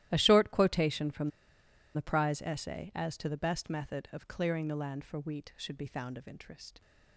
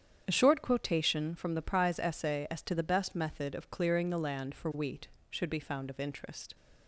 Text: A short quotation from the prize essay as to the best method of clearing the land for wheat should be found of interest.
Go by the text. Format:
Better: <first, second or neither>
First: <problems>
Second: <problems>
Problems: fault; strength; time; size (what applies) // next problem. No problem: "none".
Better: second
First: starts louder than the rest; strong; until 1.1 s; 14 dB // pauses between "from" and "the"; noticeable; at 1.2 s; 0.64 s long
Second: starts louder than the rest; strong; until 1.2 s; 8.5 dB